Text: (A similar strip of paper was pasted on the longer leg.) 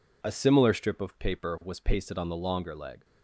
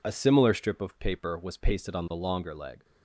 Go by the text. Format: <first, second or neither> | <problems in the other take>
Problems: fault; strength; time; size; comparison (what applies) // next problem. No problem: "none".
neither | none